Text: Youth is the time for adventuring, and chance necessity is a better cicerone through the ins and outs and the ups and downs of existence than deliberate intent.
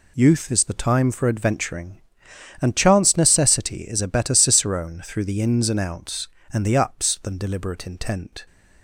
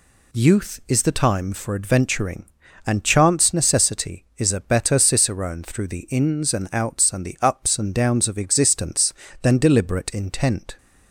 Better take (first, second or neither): second